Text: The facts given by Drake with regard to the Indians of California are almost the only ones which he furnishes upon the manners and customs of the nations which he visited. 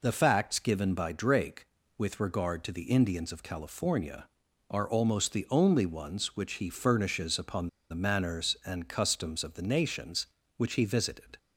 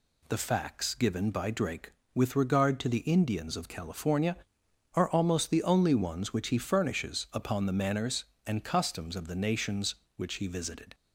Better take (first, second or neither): second